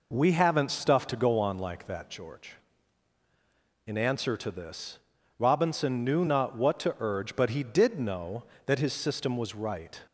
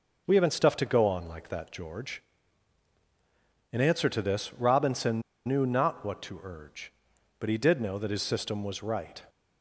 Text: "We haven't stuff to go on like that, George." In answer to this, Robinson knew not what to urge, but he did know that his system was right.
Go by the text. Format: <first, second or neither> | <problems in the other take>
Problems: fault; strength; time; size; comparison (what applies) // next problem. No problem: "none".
first | pauses between "Robinson" and "knew"; slight; at 5.2 s; 0.24 s long